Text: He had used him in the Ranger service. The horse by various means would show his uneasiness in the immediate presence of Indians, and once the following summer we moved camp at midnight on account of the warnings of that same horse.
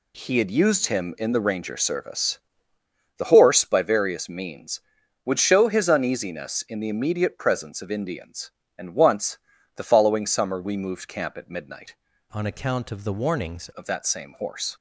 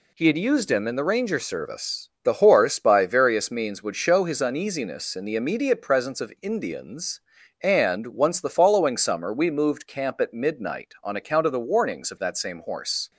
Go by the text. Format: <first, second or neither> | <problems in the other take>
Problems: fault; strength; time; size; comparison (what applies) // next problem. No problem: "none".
second | pauses between "once" and "the"; at 9.3 s; 0.38 s long // changes voice from "on" to "warnings"; from 12.3 to 13.6 s; 1.3 s long